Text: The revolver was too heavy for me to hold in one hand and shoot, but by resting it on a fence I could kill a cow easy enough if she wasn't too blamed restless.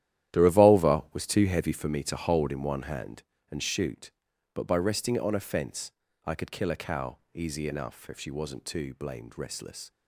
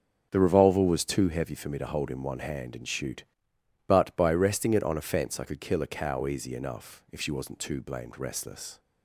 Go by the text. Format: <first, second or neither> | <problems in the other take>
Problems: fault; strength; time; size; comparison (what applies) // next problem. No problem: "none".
second | gets quieter; strong; throughout; 13 dB // starts louder than the rest; strong; until 1.4 s; 12 dB; strong in the second // pauses between "fence" and "I"; slight; at 5.8 s; 0.34 s long // pauses between "cow" and "easy"; slight; at 7.1 s; 0.16 s long